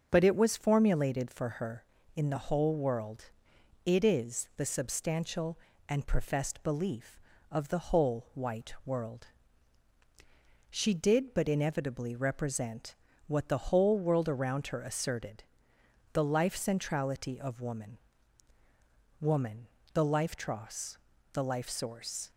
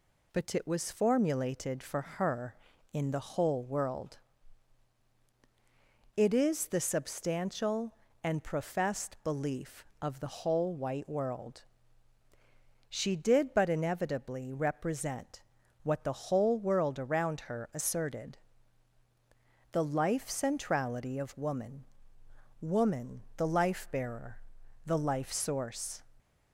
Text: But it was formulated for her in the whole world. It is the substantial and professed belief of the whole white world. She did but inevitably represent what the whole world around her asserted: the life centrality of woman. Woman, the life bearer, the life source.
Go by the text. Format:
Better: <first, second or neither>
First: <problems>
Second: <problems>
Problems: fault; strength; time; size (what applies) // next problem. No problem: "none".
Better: second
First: starts louder than the rest; until 1.1 s; 6.5 dB // pauses between "represent" and "what"; slight; at 12.9 s; 0.32 s long // says "tross" for "bearer"; at 20.3 s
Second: pauses between "represent" and "what"; at 15.4 s; 0.42 s long